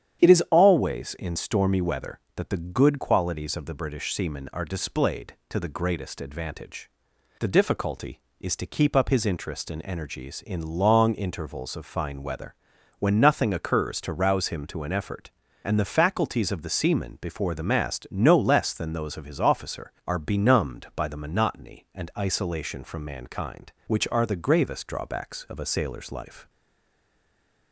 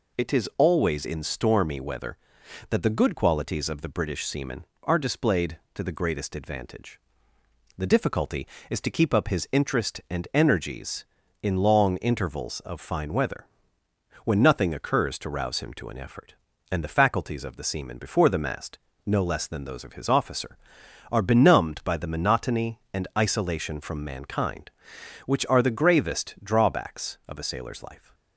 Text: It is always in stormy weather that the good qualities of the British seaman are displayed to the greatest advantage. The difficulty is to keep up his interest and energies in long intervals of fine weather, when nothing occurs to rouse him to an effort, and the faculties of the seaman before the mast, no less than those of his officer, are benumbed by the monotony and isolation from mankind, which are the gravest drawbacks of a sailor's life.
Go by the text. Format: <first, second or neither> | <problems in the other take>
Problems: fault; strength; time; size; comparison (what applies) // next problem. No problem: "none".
second | starts louder than the rest; strong; until 1.2 s; 9.5 dB // stays silent after the last word; noticeable; from 26.4 s on; 1.3 s long